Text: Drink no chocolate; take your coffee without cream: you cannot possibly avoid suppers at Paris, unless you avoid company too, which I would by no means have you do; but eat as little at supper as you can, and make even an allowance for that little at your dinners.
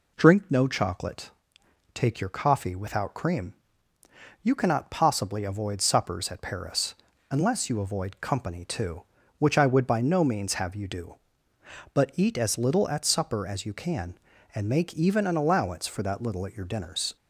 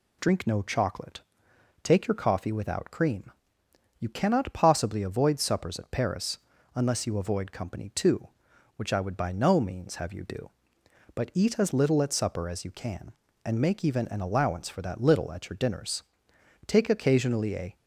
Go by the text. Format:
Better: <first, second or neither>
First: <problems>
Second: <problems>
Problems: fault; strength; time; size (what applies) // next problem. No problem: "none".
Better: first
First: none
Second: goes on to say "Take occasionally a"; noticeable; from 16.6 s on; 1.0 s long